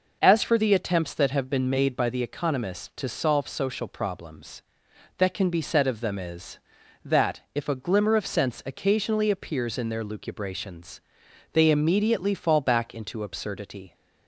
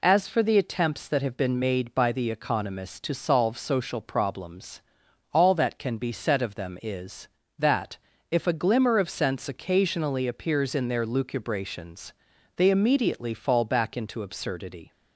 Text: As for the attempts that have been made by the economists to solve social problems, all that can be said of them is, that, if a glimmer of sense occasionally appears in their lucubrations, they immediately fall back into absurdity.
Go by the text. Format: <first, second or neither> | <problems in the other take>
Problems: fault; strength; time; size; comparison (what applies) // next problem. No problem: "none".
second | skips "all"; at 4.9 s